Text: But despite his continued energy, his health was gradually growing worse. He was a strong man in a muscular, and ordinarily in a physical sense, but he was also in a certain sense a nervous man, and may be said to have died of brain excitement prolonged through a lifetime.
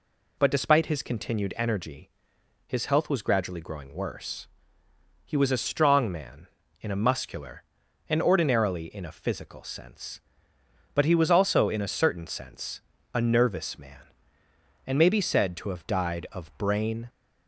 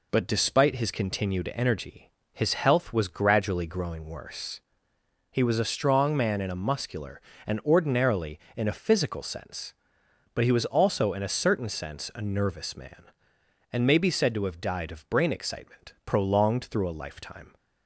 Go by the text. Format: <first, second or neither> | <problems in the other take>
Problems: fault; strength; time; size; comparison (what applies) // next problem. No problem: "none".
second | pauses between "sense" and "a"; slight; at 12.8 s; 0.32 s long // stops before "excitement prolonged through a lifetime"; at 17.0 s